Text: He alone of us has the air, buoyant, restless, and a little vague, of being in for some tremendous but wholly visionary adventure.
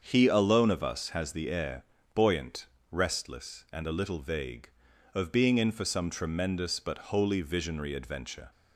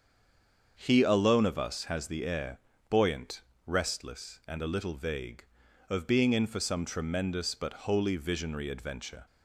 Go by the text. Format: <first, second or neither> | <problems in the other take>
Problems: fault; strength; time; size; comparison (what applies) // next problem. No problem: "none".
first | stays silent before the first word; slight; until 0.7 s; 0.7 s long // starts louder than the rest; until 1.8 s; 7 dB; also in the first